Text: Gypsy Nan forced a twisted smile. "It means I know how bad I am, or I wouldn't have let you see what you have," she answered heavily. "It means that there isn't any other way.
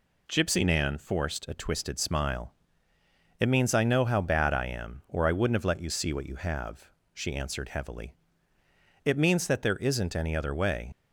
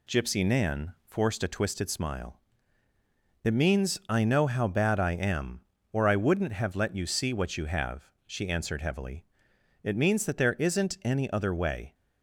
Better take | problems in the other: second | leaves "way" unfinished; at 10.9 s; 55 ms

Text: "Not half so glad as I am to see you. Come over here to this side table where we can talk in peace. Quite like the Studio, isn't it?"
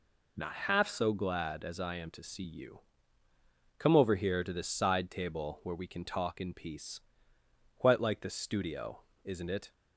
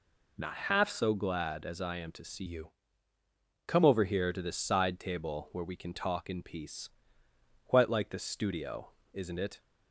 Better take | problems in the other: first | changes voice from "you" to "Come"; from 2.4 to 3.8 s; 1.4 s long

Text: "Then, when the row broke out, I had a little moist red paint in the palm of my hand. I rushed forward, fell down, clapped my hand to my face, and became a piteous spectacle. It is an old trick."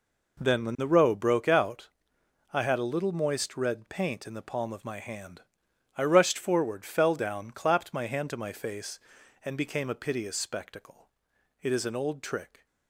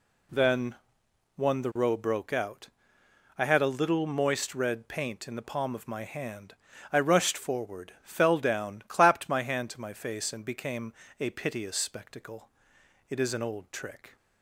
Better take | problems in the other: first | says "one" for "when"; at 1.3 s // pauses between "became" and "a"; slight; at 10.9 s; 0.28 s long

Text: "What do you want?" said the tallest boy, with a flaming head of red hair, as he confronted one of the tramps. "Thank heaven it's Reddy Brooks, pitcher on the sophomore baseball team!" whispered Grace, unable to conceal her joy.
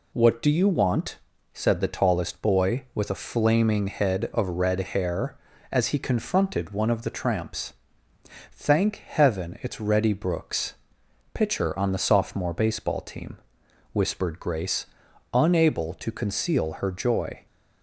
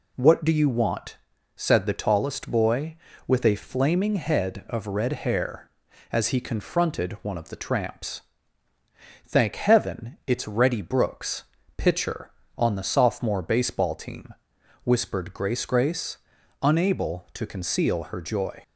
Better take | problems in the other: first | says "Grace" twice; at 15.6 s

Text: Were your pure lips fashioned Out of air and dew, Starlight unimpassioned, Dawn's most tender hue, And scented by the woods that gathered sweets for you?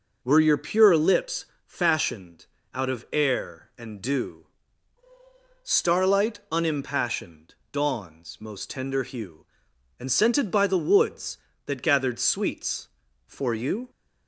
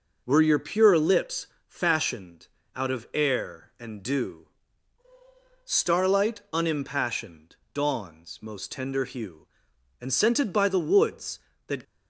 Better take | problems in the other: first | pauses between "lips" and "fashioned"; slight; at 1.4 s; 0.20 s long; slight in the first // pauses between "fashioned" and "Out"; slight; at 2.4 s; 0.28 s long; slight in the first // stops before "gathered sweets for you"; at 11.8 s

